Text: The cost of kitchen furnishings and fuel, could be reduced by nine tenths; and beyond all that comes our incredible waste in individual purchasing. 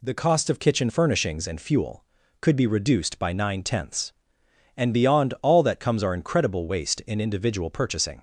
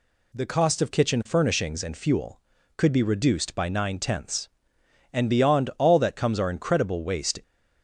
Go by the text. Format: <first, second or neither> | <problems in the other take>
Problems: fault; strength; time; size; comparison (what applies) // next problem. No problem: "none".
first | stops before "in individual purchasing"; at 7.4 s